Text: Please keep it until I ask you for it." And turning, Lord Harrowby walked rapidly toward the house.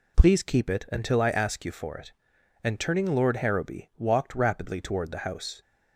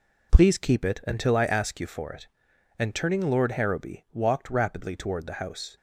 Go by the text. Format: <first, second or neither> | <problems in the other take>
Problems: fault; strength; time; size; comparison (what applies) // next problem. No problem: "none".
first | gets quieter; strong; throughout; 7 dB